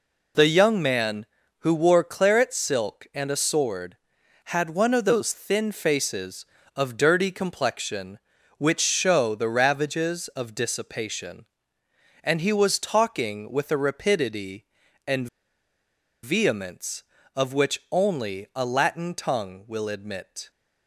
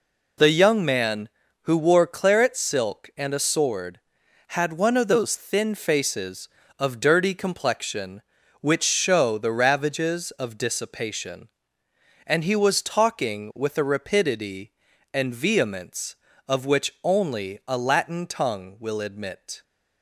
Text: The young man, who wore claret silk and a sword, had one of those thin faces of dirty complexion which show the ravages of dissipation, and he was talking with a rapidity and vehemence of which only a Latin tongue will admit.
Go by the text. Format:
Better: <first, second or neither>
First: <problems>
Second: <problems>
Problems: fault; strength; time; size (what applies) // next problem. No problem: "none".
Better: second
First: pauses between "and" and "vehemence"; noticeable; at 15.2 s; 0.97 s long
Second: none